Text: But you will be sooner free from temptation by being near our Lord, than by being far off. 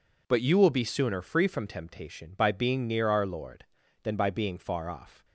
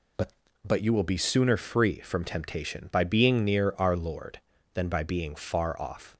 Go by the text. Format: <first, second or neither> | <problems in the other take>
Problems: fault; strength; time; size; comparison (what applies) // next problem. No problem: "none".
first | says "But" twice; at 0.6 s